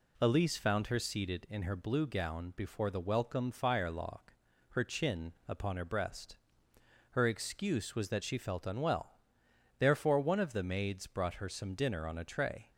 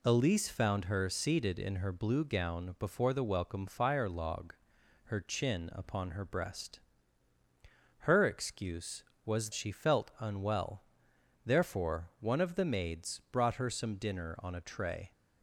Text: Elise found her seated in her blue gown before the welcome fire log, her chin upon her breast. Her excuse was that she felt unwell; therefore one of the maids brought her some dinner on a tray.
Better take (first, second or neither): first